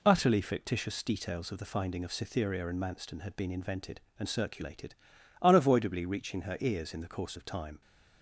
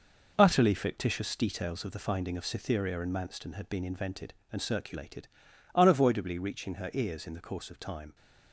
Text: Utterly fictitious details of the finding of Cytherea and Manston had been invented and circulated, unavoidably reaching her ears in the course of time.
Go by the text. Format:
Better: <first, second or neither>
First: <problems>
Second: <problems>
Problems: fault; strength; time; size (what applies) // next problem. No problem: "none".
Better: first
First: none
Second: gets quieter; strong; throughout; 7.5 dB